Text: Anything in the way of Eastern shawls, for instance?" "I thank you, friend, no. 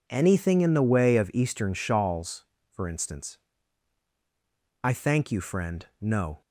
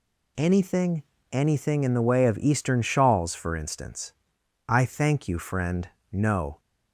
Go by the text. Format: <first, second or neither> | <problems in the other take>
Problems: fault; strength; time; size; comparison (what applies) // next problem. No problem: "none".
first | says "Anything" twice; at 1.3 s